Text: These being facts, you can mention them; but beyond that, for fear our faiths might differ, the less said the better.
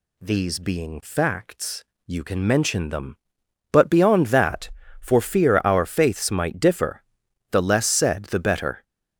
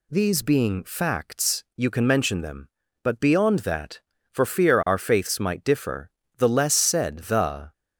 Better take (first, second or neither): first